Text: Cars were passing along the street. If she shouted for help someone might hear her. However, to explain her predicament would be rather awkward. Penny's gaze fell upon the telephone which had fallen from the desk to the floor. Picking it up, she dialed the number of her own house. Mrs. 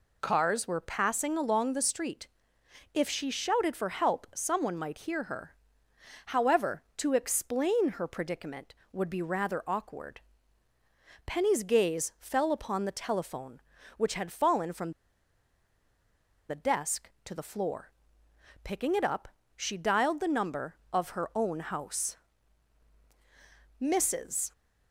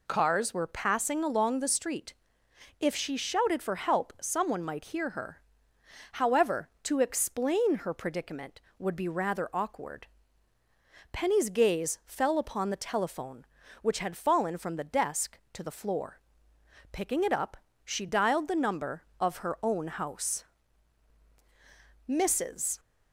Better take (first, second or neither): second